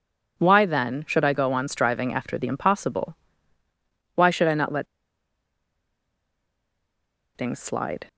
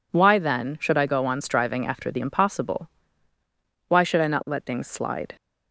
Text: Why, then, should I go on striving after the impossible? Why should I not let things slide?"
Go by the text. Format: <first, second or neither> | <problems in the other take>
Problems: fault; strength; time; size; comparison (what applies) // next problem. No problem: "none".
second | pauses between "let" and "things"; strong; at 4.8 s; 2.5 s long